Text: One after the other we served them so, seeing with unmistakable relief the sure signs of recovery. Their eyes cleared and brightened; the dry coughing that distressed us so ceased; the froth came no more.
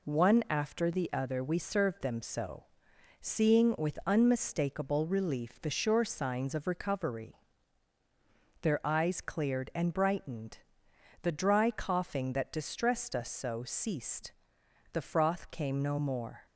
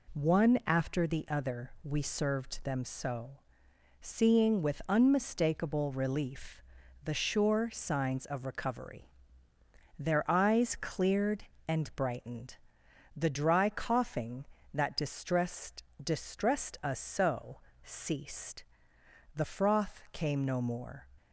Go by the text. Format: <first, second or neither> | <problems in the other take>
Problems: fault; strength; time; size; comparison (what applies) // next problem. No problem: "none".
first | pauses between "relief" and "the"; at 6.6 s; 0.40 s long // says "distressed" twice; at 16.0 s // pauses between "so" and "ceased"; slight; at 17.5 s; 0.26 s long